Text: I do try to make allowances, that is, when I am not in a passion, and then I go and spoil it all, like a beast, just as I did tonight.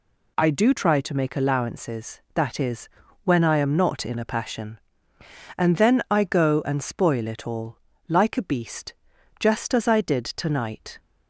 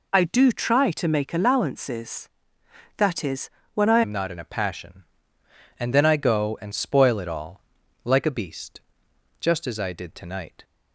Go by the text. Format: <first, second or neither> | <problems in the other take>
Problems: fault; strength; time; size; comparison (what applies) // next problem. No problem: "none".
first | changes voice at "am"; from 4.0 s on; 6.6 s long